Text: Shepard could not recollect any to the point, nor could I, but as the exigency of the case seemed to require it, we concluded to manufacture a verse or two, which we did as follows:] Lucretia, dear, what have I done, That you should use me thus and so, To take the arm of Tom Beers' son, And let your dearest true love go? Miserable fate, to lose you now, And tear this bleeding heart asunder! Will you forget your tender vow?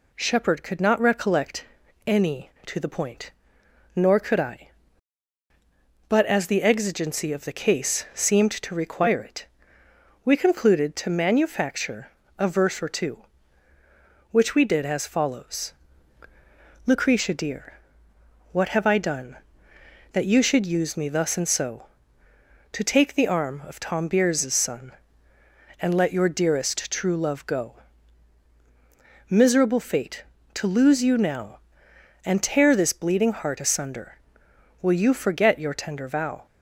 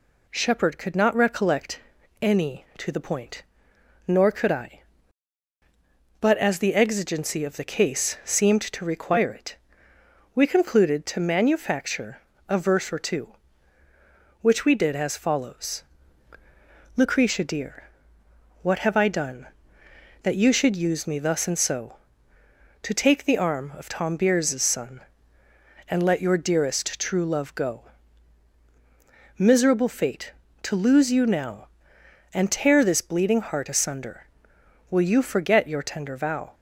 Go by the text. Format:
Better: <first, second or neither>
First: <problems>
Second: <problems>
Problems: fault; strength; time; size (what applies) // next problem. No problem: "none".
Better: neither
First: pauses between "recollect" and "any"; at 1.6 s; 0.42 s long // pauses between "manufacture" and "a"; slight; at 12.1 s; 0.26 s long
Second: pauses between "recollect" and "any"; at 1.7 s; 0.42 s long // pauses between "manufacture" and "a"; slight; at 12.2 s; 0.26 s long